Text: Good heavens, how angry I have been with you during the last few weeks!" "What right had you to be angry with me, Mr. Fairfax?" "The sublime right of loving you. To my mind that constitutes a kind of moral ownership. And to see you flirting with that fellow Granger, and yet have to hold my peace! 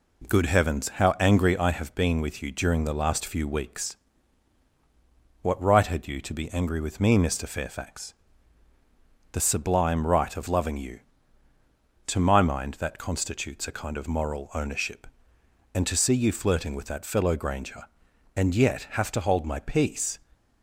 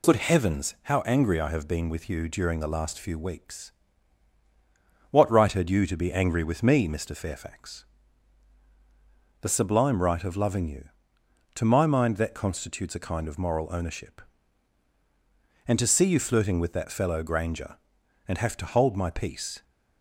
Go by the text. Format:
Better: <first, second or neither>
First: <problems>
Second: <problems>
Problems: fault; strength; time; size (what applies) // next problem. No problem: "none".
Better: first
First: none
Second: skips "yet"; at 18.3 s